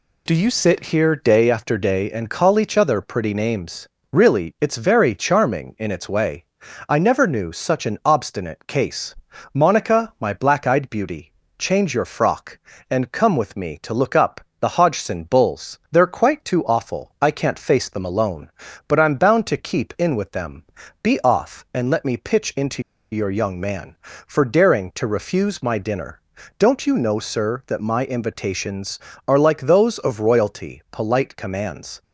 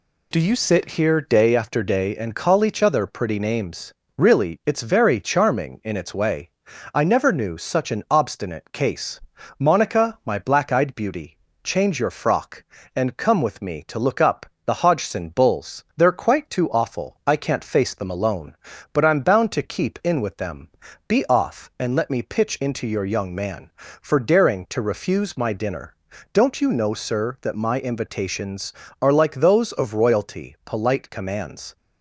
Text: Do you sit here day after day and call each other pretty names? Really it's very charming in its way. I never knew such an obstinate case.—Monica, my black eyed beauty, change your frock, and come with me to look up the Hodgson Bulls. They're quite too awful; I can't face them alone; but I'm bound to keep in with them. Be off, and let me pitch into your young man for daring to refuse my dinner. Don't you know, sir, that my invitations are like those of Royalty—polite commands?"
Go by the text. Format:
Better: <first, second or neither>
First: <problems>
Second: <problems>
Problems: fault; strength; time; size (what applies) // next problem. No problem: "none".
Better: second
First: pauses between "up" and "the"; slight; at 14.4 s; 0.18 s long // pauses between "into" and "your"; slight; at 22.8 s; 0.30 s long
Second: pauses between "up" and "the"; slight; at 14.4 s; 0.18 s long